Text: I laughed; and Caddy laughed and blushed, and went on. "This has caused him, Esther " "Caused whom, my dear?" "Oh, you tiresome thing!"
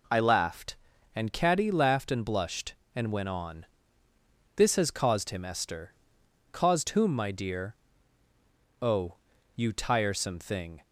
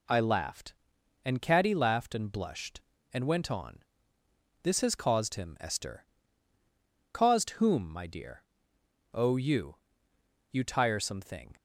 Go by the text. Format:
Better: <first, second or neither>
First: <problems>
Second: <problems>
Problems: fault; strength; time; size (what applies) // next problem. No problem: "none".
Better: first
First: none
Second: says "you" twice; at 10.5 s